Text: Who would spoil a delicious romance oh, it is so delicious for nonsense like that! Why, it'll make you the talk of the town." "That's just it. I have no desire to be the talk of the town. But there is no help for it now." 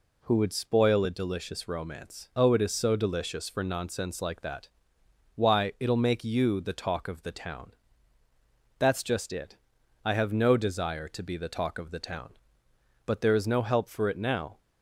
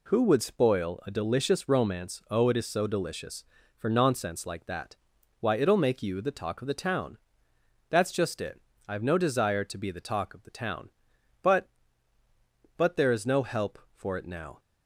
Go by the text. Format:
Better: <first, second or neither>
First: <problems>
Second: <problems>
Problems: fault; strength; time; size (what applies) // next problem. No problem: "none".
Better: first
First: none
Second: says "But" twice; at 12.7 s